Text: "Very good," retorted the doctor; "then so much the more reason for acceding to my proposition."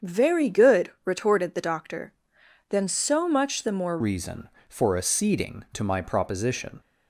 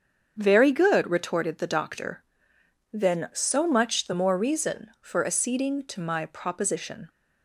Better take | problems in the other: second | starts louder than the rest; strong; until 1.1 s; 7.5 dB; strong in the second // changes voice at "reason"; from 4.0 s on; 2.8 s long

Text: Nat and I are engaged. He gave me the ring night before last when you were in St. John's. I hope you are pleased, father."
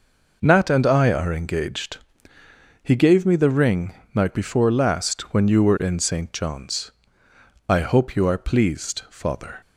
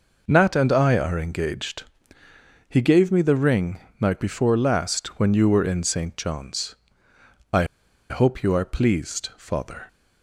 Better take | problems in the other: first | pauses between "ring" and "night"; slight; at 3.8 s; 0.20 s long; slight in the first // pauses between "I" and "hope"; at 7.6 s; 0.45 s long

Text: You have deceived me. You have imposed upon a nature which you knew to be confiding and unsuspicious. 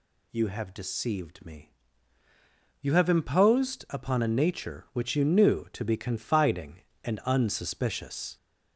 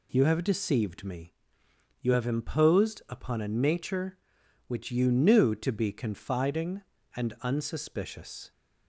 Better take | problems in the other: second | gets louder; noticeable; throughout; 4.5 dB

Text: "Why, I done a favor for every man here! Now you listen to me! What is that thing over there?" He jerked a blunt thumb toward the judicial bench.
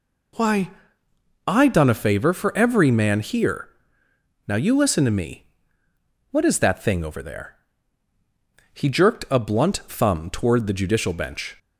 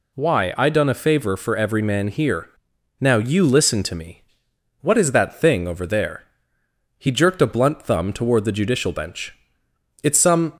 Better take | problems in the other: first | goes on to say "It's some"; slight; from 10.0 s on; 0.48 s long

